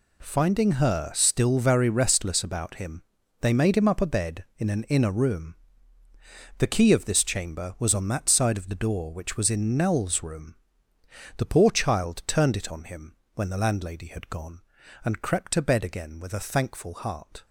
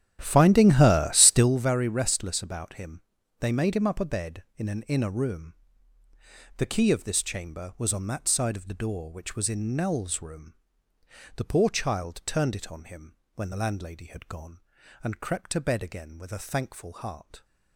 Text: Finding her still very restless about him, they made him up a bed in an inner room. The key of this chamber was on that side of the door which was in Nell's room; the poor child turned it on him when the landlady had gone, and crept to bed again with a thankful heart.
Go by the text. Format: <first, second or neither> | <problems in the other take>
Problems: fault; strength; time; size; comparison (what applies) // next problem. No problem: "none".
first | starts louder than the rest; strong; until 1.6 s; 11 dB // pauses between "him" and "when"; slight; at 13.1 s; 0.20 s long; slight in the first